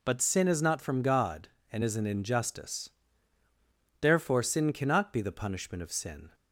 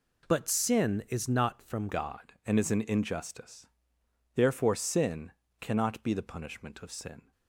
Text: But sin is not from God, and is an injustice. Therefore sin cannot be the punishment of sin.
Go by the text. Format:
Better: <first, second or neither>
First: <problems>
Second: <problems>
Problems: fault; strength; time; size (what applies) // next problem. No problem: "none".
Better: first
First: none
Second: changes voice at "God"; from 1.8 s on; 5.5 s long // pauses between "sin" and "cannot"; slight; at 5.3 s; 0.30 s long